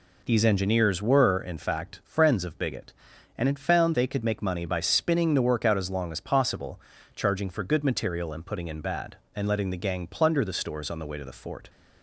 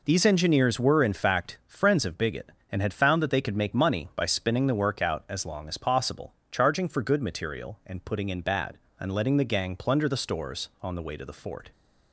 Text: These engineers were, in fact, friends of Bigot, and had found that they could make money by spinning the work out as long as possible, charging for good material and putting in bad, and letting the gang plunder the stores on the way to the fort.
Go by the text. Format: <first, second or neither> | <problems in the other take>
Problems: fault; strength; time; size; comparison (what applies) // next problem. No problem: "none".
second | skips "that"; at 3.9 s